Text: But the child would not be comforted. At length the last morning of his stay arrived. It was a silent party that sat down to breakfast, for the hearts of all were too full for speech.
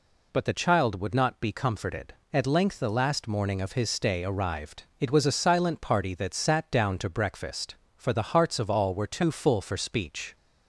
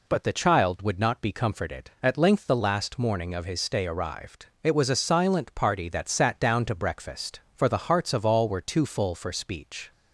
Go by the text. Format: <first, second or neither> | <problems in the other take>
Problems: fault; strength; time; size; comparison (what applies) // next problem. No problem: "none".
neither | none